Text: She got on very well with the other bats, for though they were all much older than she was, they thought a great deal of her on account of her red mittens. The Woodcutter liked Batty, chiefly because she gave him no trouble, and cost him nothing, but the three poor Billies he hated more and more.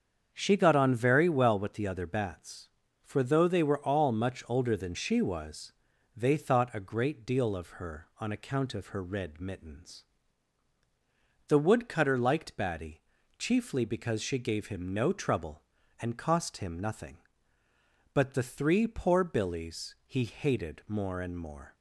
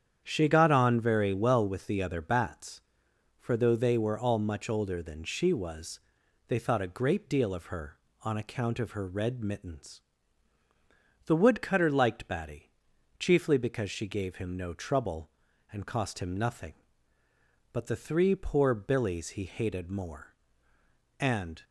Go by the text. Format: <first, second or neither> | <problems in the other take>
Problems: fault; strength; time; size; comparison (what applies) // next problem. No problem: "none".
first | starts louder than the rest; strong; until 1.2 s; 8.5 dB; strong in the first // stops before "more"; at 21.6 s